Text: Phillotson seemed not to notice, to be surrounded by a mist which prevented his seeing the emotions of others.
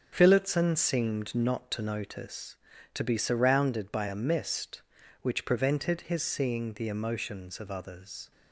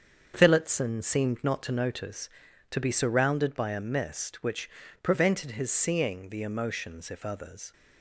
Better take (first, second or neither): first